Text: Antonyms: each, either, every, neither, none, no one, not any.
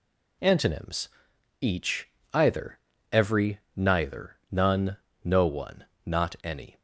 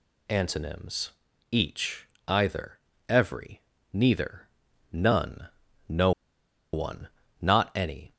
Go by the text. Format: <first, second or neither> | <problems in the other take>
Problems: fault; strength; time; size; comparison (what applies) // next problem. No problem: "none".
first | pauses between "no" and "one"; noticeable; at 6.1 s; 0.62 s long